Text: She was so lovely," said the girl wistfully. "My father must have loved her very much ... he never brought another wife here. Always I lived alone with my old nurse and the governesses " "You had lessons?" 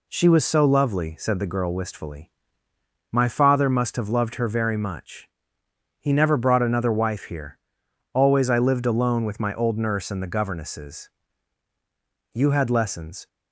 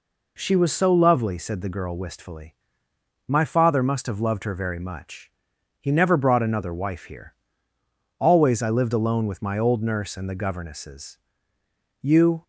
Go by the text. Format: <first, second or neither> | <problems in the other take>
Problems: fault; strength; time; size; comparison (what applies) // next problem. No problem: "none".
first | stops before "had lessons"; at 12.4 s